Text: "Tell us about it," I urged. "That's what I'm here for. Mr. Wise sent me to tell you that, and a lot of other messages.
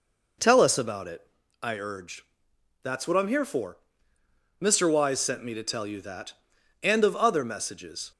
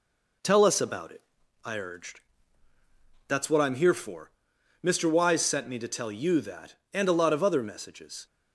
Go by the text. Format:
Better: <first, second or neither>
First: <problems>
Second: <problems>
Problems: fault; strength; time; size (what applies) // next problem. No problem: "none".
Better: second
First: skips "a lot"; at 7.0 s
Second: none